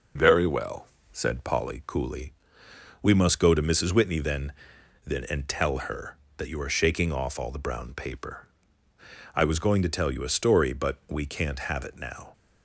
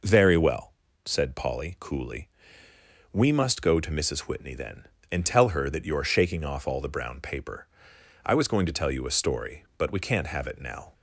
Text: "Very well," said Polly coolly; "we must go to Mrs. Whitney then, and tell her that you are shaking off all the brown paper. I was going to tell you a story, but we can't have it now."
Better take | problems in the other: second | says "then" twice; at 5.0 s

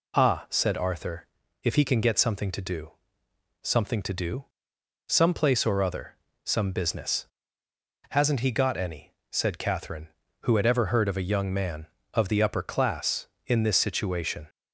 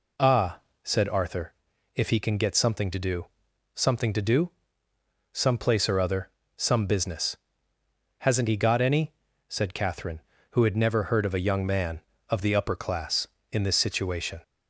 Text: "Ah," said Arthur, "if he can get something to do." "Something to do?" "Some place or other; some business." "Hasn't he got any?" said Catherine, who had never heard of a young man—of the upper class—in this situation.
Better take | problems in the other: second | says "ever" for "never"; at 10.6 s

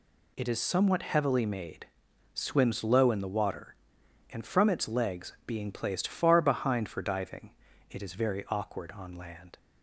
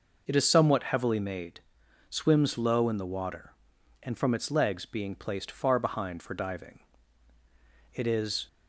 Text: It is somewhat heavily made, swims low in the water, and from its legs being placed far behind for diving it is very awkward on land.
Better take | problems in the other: first | pauses between "diving" and "it"; at 6.7 s; 1.1 s long; slight in the first // stops before "very awkward on land"; at 8.4 s

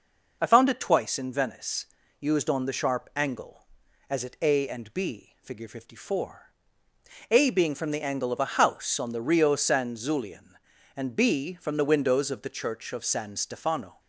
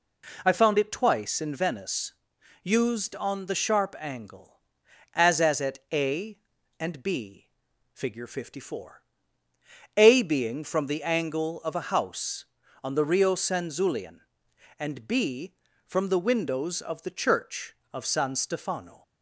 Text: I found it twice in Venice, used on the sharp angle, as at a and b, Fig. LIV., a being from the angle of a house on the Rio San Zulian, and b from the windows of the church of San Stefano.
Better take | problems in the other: first | says "as" twice; at 5.4 s

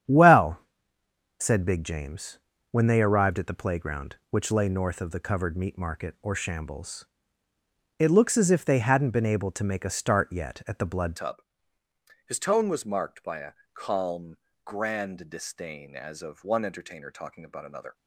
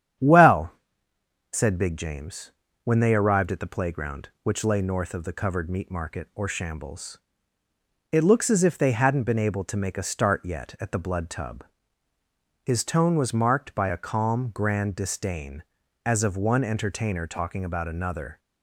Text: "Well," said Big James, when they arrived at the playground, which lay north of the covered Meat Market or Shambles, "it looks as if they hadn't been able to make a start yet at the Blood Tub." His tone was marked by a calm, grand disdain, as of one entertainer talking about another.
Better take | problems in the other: second | starts louder than the rest; strong; until 1.8 s; 9 dB; strong in the second // changes voice at "Tub"; from 11.1 s on; 6.8 s long // pauses between "a" and "calm"; slight; at 13.5 s; 0.20 s long

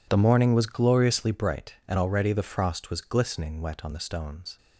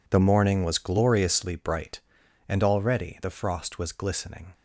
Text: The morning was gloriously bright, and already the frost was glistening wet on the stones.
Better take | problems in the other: first | stops before "wet on the stones"; at 4.5 s

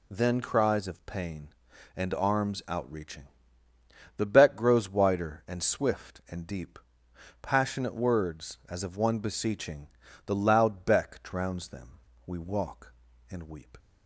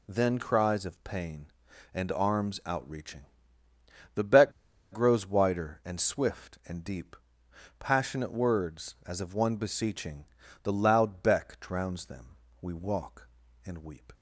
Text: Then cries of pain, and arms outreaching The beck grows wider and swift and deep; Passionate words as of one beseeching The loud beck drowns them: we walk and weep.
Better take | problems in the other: first | pauses between "outreaching" and "The"; noticeable; at 3.2 s; 0.90 s long; noticeable in the first // pauses between "beck" and "grows"; at 4.5 s; 0.39 s long // pauses between "beseeching" and "The"; at 10.2 s; 0.38 s long; also in the first

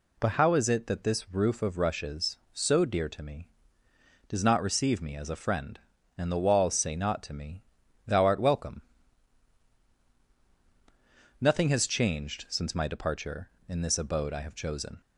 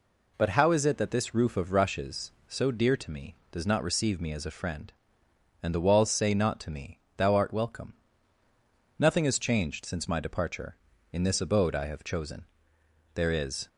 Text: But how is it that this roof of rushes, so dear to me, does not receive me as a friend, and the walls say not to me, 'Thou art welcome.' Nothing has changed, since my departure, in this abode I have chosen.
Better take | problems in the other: first | goes on to say "There is"; from 13.1 s on; 0.54 s long

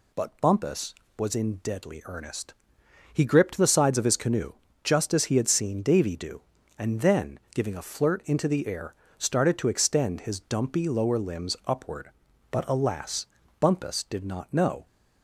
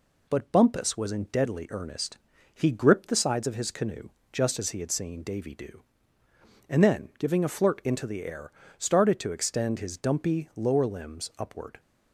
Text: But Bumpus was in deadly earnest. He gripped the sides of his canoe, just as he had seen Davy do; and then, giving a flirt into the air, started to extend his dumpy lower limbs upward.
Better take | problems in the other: second | goes on to say "But alas Bumpus did not know"; strong; from 12.5 s on; 2.3 s long

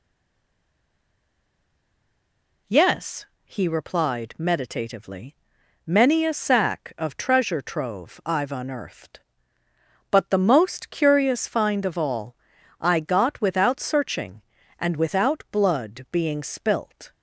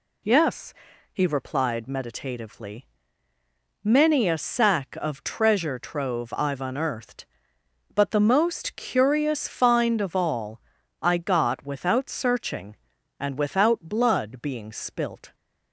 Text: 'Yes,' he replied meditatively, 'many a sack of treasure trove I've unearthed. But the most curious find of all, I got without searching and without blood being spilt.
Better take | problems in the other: second | stays silent before the first word; strong; until 2.6 s; 2.6 s long

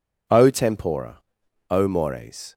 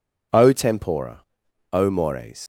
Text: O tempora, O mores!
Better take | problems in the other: first | leaves "mores" unfinished; at 2.4 s; 95 ms

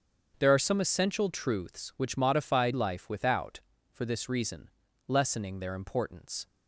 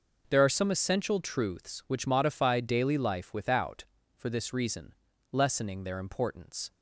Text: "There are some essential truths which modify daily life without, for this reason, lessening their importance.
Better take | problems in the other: second | starts louder than the rest; strong; until 1.3 s; 7 dB // skips "daily"; at 2.7 s

